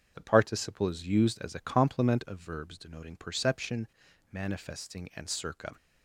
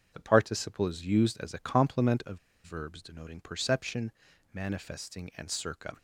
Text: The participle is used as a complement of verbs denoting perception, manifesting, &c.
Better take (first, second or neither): first